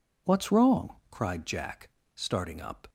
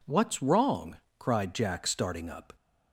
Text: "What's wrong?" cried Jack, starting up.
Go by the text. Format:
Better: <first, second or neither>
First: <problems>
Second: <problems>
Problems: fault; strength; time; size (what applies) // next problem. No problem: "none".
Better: neither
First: none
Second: none